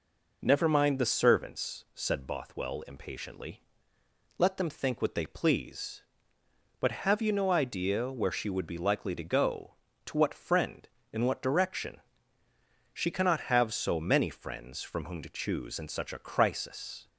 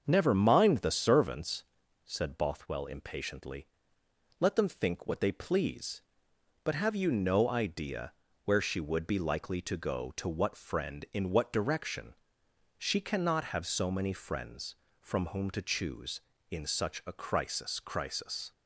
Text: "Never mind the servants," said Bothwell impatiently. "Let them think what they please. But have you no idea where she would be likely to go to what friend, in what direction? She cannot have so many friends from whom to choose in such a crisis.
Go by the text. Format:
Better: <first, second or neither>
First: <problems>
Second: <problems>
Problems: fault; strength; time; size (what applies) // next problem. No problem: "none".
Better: first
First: none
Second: starts louder than the rest; until 1.0 s; 6.5 dB // pauses between "idea" and "where"; slight; at 8.1 s; 0.32 s long // says "crisis" twice; at 17.7 s